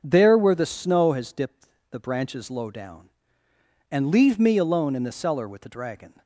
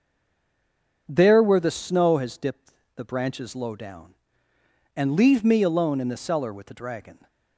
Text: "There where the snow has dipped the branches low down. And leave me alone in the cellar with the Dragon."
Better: first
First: starts louder than the rest; until 1.0 s; 6 dB // pauses between "dipped" and "the"; slight; at 1.6 s; 0.24 s long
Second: stays silent before the first word; until 1.0 s; 1.0 s long // starts louder than the rest; until 2.0 s; 6 dB // pauses between "dipped" and "the"; slight; at 2.7 s; 0.24 s long

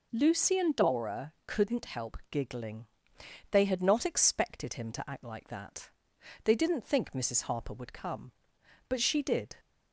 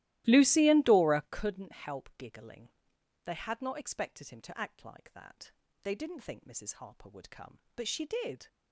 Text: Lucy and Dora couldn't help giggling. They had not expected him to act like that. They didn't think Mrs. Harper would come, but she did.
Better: first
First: none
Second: starts louder than the rest; strong; until 1.4 s; 15.5 dB

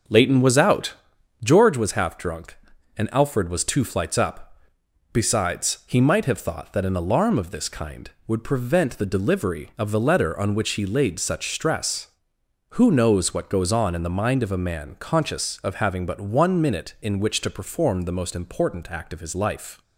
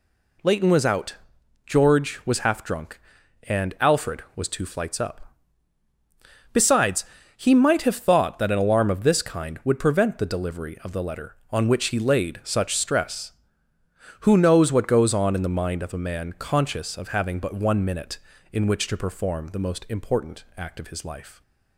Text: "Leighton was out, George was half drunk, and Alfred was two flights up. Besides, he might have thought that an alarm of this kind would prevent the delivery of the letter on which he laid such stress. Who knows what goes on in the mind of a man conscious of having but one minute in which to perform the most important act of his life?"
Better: second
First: starts louder than the rest; until 1.6 s; 6.5 dB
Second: none

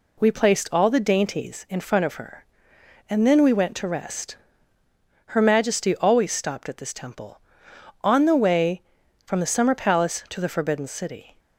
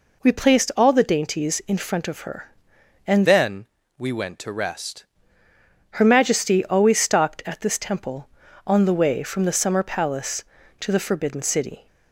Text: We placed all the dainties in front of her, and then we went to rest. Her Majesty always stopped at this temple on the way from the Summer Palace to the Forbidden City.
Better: first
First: none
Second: changes voice from "then" to "rest"; from 3.2 to 5.0 s; 1.8 s long // pauses between "then" and "we"; slight; at 3.6 s; 0.32 s long

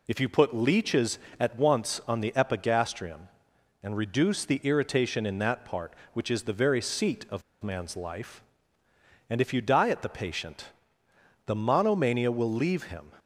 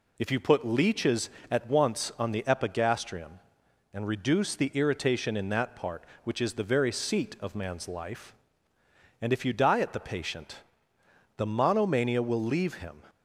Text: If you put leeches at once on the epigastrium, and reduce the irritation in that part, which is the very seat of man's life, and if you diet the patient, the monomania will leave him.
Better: second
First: pauses between "of" and "man's"; slight; at 7.4 s; 0.20 s long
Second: none

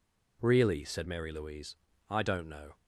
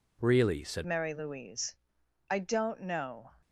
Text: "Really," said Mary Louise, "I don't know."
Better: first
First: none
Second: changes voice at "Mary"; from 0.8 s on; 2.5 s long

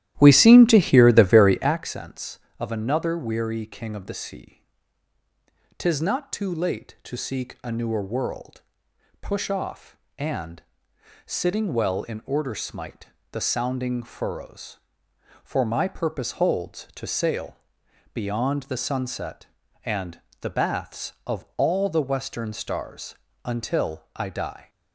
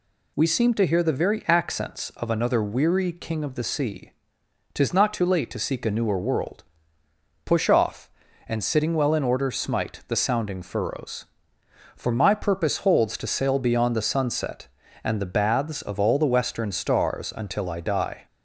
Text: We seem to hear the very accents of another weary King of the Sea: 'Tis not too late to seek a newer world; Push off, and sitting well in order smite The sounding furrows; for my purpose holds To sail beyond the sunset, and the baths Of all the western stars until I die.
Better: second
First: starts louder than the rest; strong; until 1.8 s; 13 dB // pauses between "and" and "sitting"; noticeable; at 10.6 s; 0.62 s long // pauses between "smite" and "The"; slight; at 13.0 s; 0.26 s long // pauses between "sail" and "beyond"; noticeable; at 17.5 s; 0.56 s long // pauses between "and" and "the"; slight; at 20.2 s; 0.18 s long // pauses between "stars" and "until"; slight; at 23.1 s; 0.28 s long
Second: none

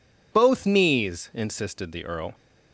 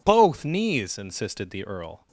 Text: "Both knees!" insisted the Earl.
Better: neither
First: none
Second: none

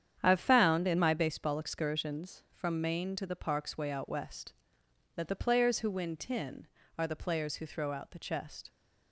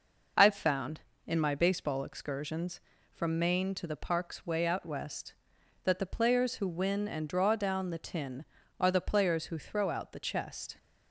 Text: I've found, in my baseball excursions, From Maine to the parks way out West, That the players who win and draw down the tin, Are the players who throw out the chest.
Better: second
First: starts louder than the rest; strong; until 1.2 s; 9 dB // skips "and draw down the"; at 6.1 s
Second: none

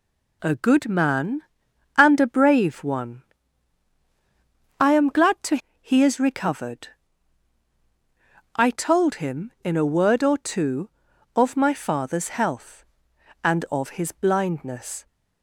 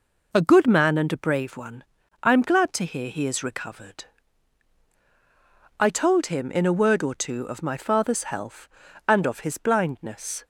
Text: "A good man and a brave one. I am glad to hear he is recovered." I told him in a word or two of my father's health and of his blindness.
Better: second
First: skips "hear"; at 5.6 s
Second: none

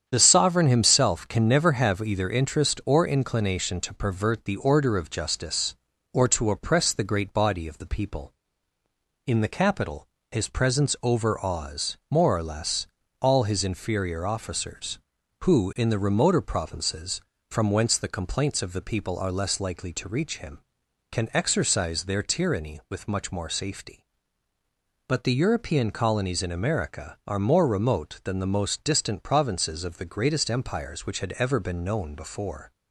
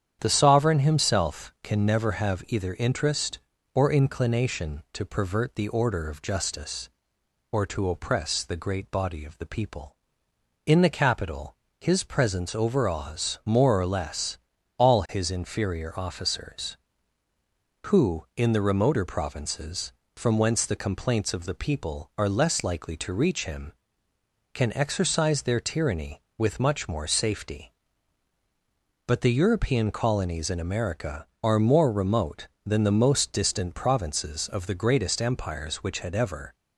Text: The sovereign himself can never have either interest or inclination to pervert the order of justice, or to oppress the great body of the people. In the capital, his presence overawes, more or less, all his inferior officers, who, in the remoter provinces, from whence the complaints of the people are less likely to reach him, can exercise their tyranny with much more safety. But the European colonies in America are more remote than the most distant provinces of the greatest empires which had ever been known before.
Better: first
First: starts louder than the rest; strong; until 1.0 s; 8.5 dB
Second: starts louder than the rest; strong; until 1.2 s; 9 dB // stops before "been known before"; at 36.5 s

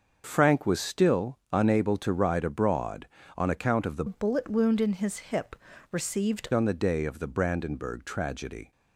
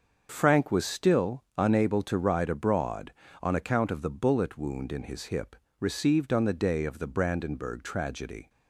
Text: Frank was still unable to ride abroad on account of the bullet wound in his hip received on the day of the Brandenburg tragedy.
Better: second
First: starts louder than the rest; until 1.2 s; 6.5 dB // pauses between "still" and "unable"; slight; at 1.3 s; 0.16 s long // changes voice from "bullet" to "received"; from 4.0 to 6.4 s; 2.4 s long // pauses between "hip" and "received"; slight; at 5.5 s; 0.36 s long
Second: starts louder than the rest; until 1.3 s; 6.5 dB // pauses between "still" and "unable"; slight; at 1.4 s; 0.16 s long // pauses between "hip" and "received"; slight; at 5.5 s; 0.24 s long

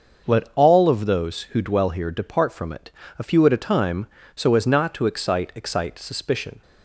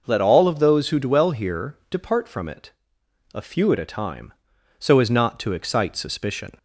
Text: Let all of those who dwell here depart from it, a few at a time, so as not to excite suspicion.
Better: second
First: starts louder than the rest; until 1.3 s; 6.5 dB // says "excite" twice; at 5.5 s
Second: none

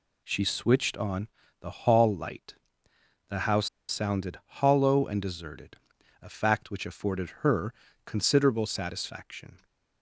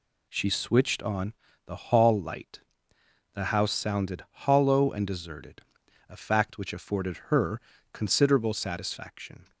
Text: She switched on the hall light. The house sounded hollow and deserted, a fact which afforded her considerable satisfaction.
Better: second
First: pauses between "on" and "the"; slight; at 1.2 s; 0.32 s long // pauses between "house" and "sounded"; slight; at 3.6 s; 0.20 s long // pauses between "her" and "considerable"; slight; at 7.7 s; 0.32 s long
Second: pauses between "on" and "the"; slight; at 1.3 s; 0.32 s long // pauses between "her" and "considerable"; slight; at 7.5 s; 0.32 s long

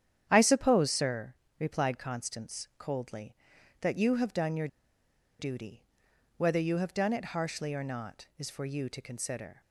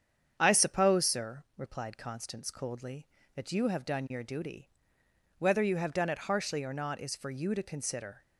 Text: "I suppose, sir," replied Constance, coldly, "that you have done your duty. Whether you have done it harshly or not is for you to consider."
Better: second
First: starts louder than the rest; strong; until 1.2 s; 9.5 dB // pauses between "your" and "duty"; noticeable; at 4.6 s; 0.72 s long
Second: starts louder than the rest; strong; until 1.3 s; 8 dB

